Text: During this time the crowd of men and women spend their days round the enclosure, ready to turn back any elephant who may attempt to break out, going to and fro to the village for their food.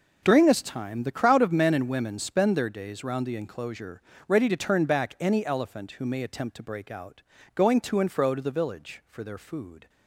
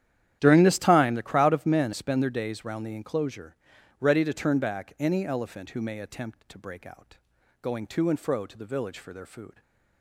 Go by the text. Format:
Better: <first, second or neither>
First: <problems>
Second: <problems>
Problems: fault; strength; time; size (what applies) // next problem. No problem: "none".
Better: first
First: none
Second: starts louder than the rest; strong; until 1.4 s; 11 dB // skips "and women"; at 1.9 s // stays silent after the last word; slight; from 9.5 s on; 0.5 s long